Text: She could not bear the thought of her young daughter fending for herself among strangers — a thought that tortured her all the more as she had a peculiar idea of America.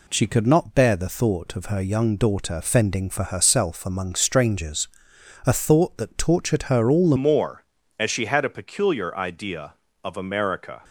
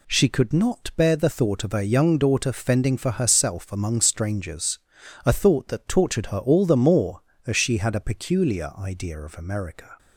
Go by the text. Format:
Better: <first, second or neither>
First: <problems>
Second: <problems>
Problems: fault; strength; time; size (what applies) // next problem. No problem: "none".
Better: second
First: changes voice at "more"; from 7.1 s on; 3.7 s long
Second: none